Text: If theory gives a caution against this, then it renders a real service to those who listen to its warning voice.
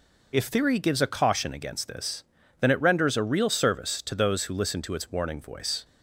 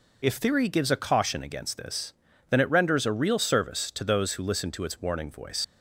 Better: first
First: none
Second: leaves "voice" unfinished; at 5.6 s; 95 ms

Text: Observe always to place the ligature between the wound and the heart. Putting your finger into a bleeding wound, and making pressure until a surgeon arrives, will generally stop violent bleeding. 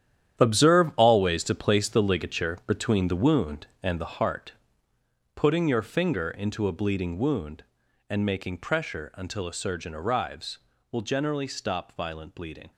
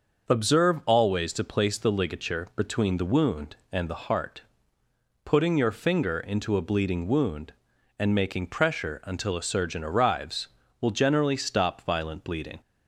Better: second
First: gets quieter; strong; throughout; 11 dB // starts louder than the rest; strong; until 1.4 s; 10.5 dB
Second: starts louder than the rest; until 1.3 s; 6 dB

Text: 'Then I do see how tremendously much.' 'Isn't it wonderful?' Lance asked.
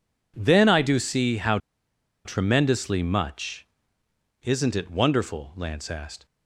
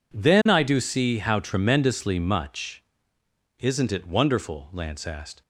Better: second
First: pauses between "how" and "tremendously"; noticeable; at 1.5 s; 0.66 s long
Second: none

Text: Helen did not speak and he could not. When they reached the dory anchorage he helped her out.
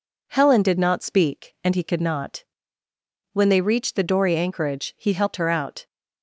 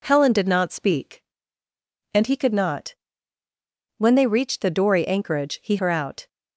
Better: first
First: none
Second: skips "helped"; at 5.7 s

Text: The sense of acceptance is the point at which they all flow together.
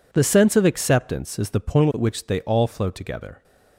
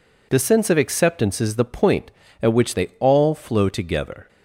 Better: neither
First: none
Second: none

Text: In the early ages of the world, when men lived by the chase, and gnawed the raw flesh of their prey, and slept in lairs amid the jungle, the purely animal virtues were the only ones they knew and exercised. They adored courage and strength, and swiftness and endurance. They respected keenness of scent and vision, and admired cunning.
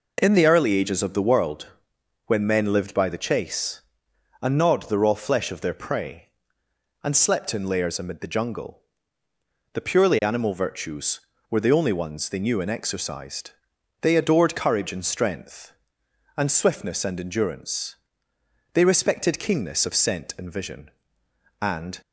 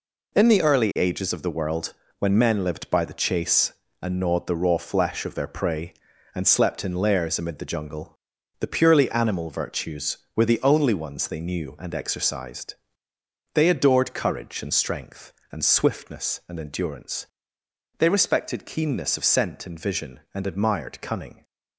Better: second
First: stops before "admired cunning"; at 22.0 s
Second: none

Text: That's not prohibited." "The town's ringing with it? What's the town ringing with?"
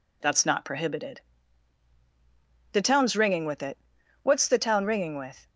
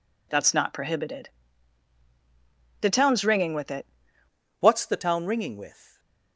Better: first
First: none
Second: changes voice at "What's"; from 4.6 s on; 1.3 s long // stays silent after the last word; slight; from 5.7 s on; 0.6 s long

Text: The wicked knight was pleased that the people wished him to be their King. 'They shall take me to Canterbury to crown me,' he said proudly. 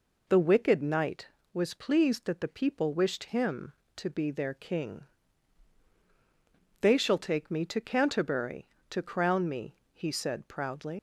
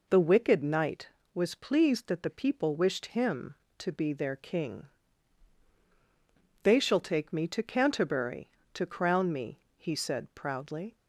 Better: second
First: leaves "proudly" unfinished; at 10.9 s; 110 ms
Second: none

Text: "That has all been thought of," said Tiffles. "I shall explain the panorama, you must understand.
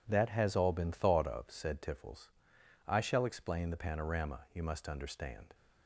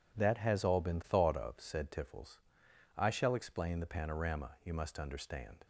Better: neither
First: none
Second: none

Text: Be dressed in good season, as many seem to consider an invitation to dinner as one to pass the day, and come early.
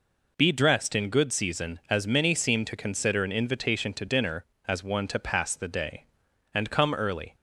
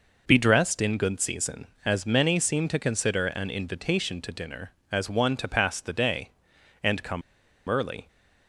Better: first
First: none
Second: pauses between "come" and "early"; noticeable; at 7.2 s; 0.46 s long

